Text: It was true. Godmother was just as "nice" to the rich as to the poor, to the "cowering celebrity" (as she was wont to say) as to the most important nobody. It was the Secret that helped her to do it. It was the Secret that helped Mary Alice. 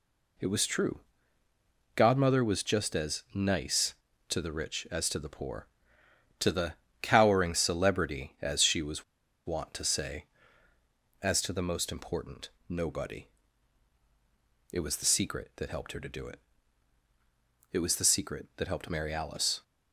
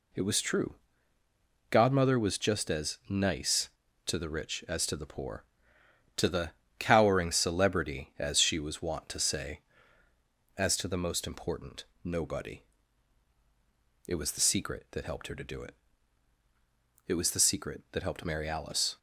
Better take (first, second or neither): second